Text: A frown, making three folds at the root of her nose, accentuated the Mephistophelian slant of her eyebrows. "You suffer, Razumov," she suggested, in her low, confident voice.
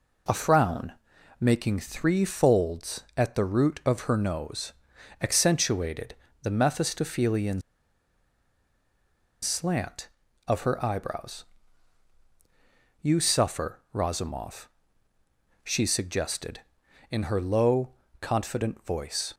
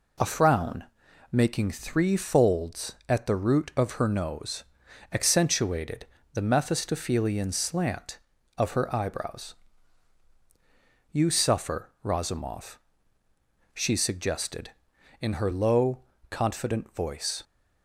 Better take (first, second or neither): second